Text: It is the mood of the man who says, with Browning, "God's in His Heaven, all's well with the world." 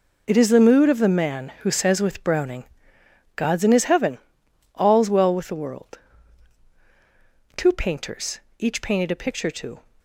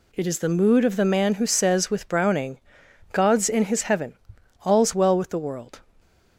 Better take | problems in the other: second | goes on to say "Two painters each painted a picture to"; strong; from 7.5 s on; 2.2 s long

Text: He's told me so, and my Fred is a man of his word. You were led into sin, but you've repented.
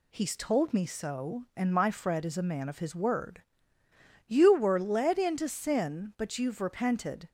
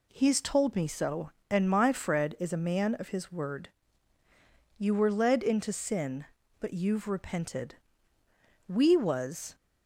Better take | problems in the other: first | goes on to say "We was"; noticeable; from 8.6 s on; 0.88 s long

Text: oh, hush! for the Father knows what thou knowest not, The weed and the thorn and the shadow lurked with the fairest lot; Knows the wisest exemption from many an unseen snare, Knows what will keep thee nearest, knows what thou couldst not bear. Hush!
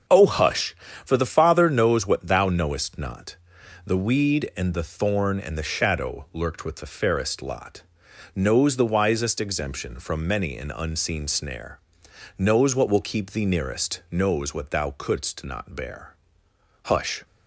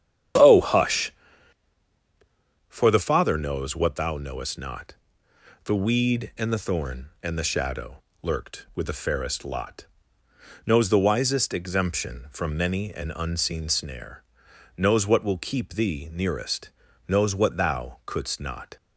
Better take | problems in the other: first | starts louder than the rest; strong; until 2.9 s; 9.5 dB; also in the first // pauses between "shadow" and "lurked"; slight; at 8.0 s; 0.18 s long // stops before "bear Hush"; at 18.7 s

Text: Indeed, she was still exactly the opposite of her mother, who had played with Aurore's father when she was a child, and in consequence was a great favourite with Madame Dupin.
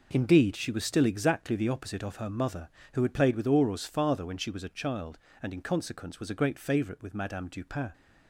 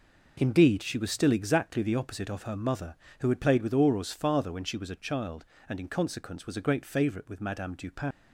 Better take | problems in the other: first | leaves "Dupin" unfinished; at 8.1 s; 85 ms

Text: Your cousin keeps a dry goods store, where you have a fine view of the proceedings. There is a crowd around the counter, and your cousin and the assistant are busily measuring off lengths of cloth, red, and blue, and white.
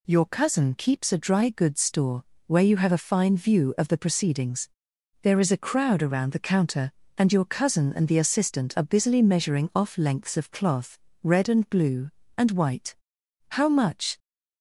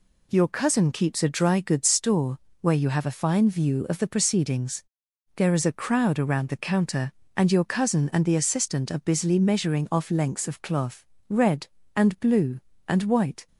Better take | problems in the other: second | goes on to say "How much"; noticeable; from 13.5 s on; 0.66 s long

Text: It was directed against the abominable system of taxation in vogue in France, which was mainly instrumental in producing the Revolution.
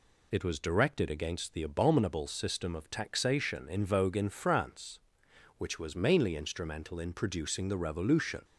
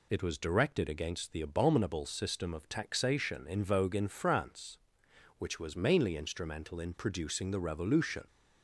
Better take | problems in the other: neither | none

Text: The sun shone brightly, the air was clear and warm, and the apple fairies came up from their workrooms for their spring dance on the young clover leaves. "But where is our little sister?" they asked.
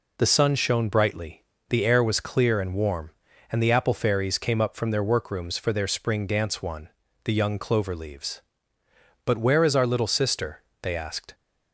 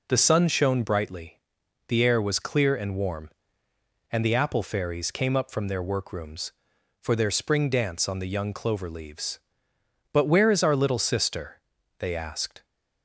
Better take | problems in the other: second | says "one" for "on"; at 6.6 s

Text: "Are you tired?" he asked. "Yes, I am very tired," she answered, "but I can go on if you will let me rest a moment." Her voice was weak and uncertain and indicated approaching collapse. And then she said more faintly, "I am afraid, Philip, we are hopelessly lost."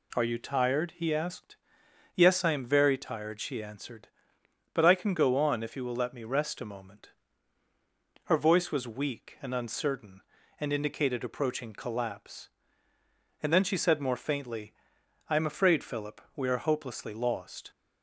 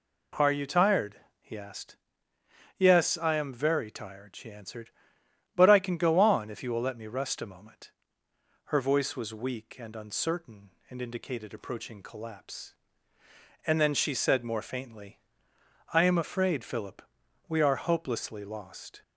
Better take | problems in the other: neither | none

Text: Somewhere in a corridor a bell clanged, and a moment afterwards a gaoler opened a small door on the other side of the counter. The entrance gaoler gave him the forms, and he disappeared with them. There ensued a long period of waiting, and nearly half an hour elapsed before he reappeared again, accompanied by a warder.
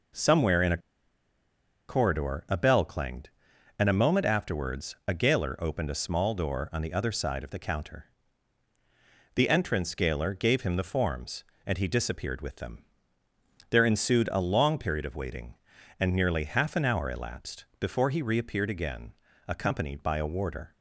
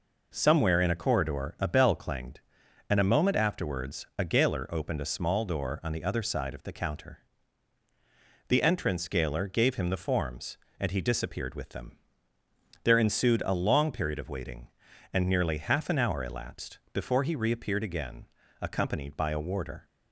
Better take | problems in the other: second | pauses between "a" and "corridor"; at 0.7 s; 1.1 s long

